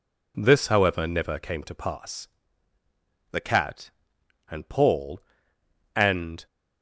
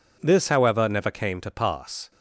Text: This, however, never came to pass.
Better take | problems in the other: second | goes on to say "The cat and Paul and"; strong; from 3.3 s on; 3.1 s long

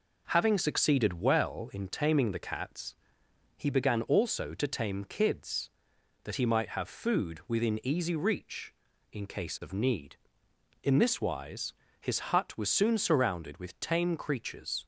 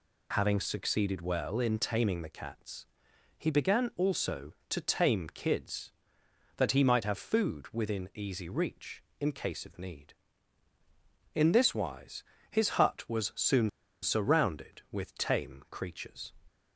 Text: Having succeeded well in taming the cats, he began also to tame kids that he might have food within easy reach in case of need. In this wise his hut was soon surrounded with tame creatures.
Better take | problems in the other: first | pauses between "wise" and "his"; slight; at 12.2 s; 0.26 s long; slight in the first // pauses between "soon" and "surrounded"; slight; at 13.6 s; 0.33 s long

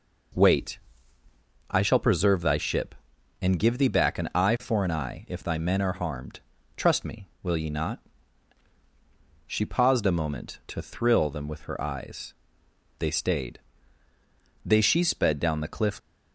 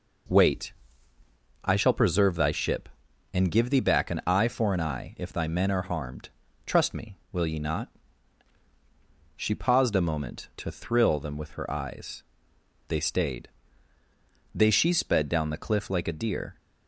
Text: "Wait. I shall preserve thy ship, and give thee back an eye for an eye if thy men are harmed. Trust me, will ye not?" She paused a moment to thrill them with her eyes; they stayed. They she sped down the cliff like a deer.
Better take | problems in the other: second | stops before "like a deer"; at 15.9 s

